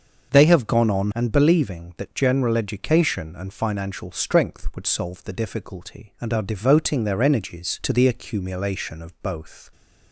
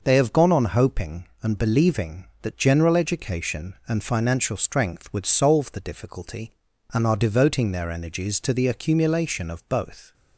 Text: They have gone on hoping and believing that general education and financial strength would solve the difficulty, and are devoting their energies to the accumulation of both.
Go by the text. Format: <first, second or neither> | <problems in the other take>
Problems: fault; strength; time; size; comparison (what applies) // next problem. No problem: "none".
second | starts louder than the rest; until 1.3 s; 6.5 dB // skips "hoping"; at 1.1 s